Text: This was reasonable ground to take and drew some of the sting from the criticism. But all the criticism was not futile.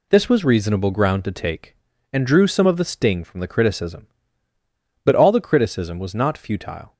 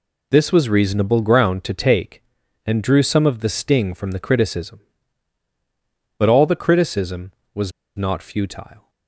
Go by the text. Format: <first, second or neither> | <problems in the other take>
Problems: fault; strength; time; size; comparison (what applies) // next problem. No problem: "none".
first | pauses between "was" and "not"; slight; at 7.7 s; 0.25 s long